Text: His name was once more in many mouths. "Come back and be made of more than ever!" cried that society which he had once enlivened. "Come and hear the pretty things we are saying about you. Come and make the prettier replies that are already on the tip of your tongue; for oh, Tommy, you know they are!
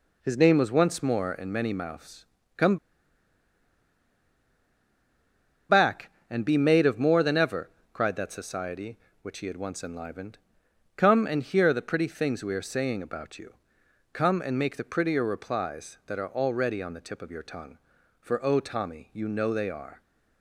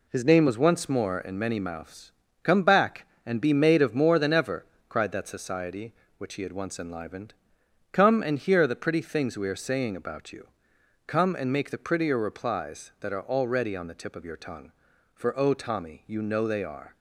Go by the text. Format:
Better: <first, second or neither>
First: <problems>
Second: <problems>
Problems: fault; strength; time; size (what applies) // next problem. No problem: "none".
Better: second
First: pauses between "Come" and "back"; strong; at 2.7 s; 2.9 s long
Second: none